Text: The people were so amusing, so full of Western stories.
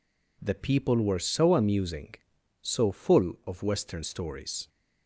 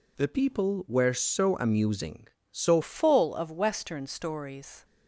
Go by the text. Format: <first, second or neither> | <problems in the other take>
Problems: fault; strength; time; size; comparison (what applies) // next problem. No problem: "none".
first | changes voice at "full"; from 2.8 s on; 2.0 s long